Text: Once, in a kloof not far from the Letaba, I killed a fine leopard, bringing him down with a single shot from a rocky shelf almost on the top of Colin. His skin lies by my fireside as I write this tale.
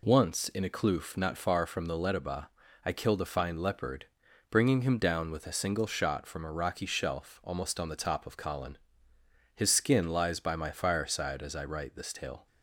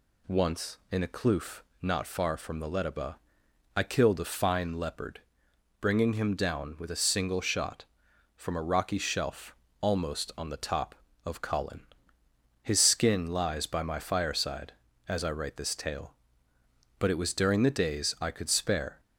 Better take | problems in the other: first | pauses between "kloof" and "not"; slight; at 1.6 s; 0.20 s long // pauses between "shelf" and "almost"; slight; at 9.5 s; 0.28 s long // goes on to say "But it was during the days I could spare"; strong; from 16.9 s on; 2.0 s long

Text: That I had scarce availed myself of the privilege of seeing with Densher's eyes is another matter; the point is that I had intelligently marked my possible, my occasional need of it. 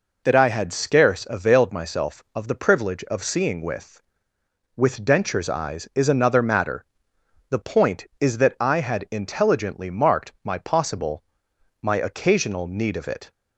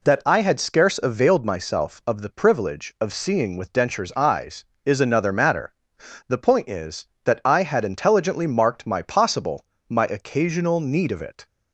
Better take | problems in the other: second | says "with" twice; at 4.7 s

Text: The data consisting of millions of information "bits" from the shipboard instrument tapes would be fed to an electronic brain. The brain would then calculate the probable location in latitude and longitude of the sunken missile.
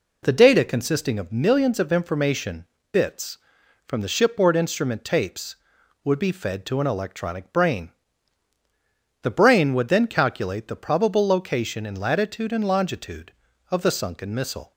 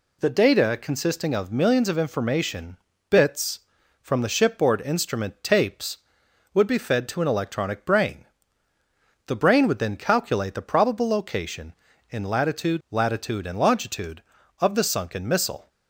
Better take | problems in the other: first | pauses between "information" and "bits"; slight; at 2.7 s; 0.34 s long; slight in the first // says "latitude" twice; at 12.9 s

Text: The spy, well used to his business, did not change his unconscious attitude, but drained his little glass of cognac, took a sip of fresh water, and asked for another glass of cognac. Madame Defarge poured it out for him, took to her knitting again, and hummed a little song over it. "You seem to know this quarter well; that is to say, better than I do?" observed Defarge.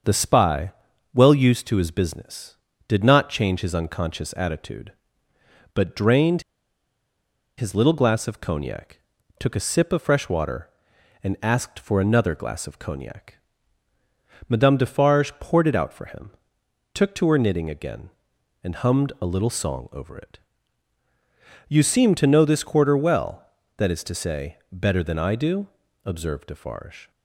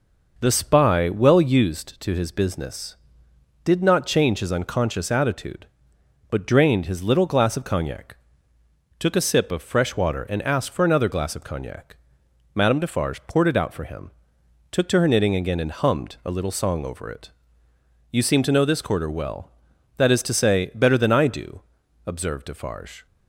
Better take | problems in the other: second | starts louder than the rest; until 1.4 s; 7 dB // pauses between "drained" and "his"; at 6.4 s; 1.1 s long

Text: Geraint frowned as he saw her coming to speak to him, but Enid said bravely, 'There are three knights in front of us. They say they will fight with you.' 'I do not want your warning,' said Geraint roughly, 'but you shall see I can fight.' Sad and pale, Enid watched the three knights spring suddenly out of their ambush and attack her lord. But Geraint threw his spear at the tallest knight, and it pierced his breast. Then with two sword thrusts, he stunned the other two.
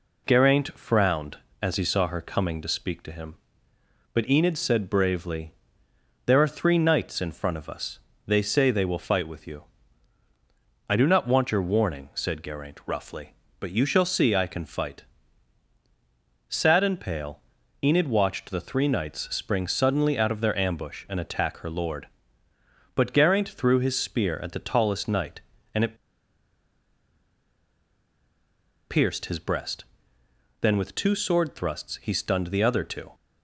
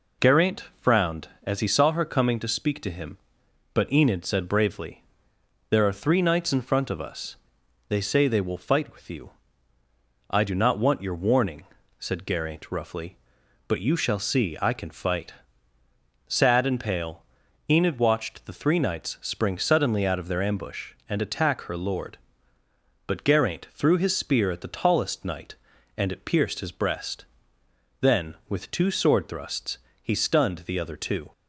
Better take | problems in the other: second | pauses between "it" and "pierced"; strong; at 25.9 s; 2.9 s long

